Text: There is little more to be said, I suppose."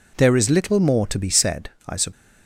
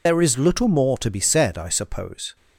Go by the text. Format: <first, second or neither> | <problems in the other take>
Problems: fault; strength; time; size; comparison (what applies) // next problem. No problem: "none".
first | loses the start of "There"; at 0.0 s; 90 ms